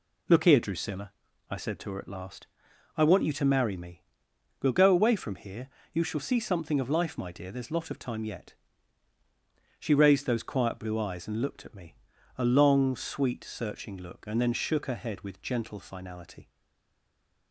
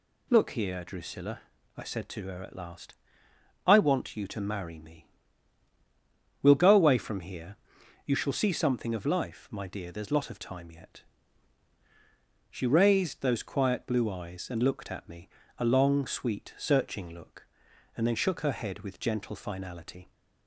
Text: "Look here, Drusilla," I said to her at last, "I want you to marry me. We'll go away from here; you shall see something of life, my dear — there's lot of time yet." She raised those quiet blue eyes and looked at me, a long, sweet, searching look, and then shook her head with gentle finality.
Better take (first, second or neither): second